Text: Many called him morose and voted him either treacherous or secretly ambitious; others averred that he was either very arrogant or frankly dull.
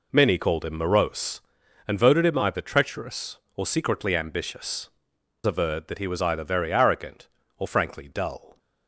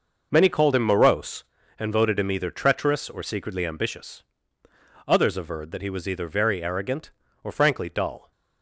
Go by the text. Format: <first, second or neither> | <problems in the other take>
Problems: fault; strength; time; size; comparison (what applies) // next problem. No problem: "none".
second | skips "others"; at 5.1 s